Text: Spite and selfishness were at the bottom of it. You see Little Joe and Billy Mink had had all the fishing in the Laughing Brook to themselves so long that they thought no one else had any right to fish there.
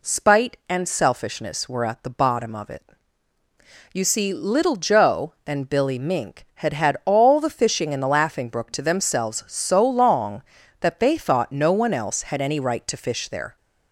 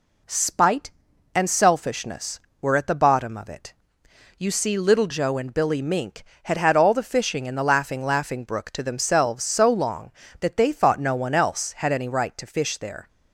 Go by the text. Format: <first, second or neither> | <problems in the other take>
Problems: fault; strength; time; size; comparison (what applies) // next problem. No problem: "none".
first | says "Laughing" twice; at 8.0 s